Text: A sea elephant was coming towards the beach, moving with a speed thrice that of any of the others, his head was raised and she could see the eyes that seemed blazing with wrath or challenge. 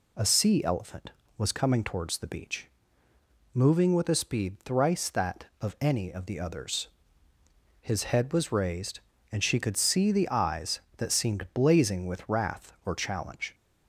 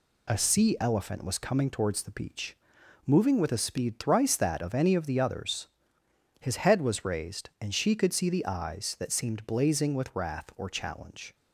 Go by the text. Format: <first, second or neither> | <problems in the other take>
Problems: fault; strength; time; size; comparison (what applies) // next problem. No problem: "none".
neither | none